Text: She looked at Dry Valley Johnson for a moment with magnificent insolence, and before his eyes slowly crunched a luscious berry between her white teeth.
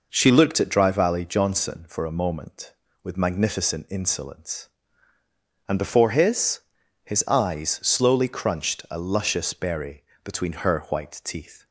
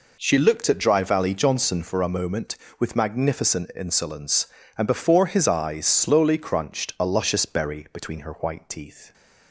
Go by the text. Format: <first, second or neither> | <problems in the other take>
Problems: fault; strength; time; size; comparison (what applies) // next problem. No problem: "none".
second | says "his" twice; at 7.0 s // pauses between "berry" and "between"; slight; at 10.0 s; 0.22 s long